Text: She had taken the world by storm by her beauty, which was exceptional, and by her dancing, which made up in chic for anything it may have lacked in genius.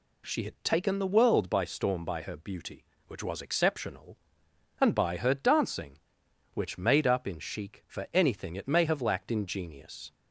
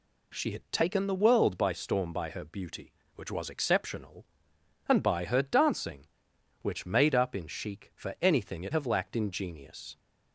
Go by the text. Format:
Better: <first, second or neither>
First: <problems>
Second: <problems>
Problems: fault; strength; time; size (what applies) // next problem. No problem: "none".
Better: first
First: none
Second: skips "may"; at 8.7 s